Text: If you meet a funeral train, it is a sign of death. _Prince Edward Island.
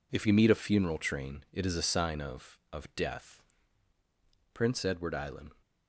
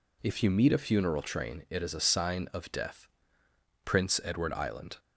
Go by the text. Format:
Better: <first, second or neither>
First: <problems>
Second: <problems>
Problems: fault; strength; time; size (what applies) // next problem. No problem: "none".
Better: second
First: says "of" twice; at 2.7 s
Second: none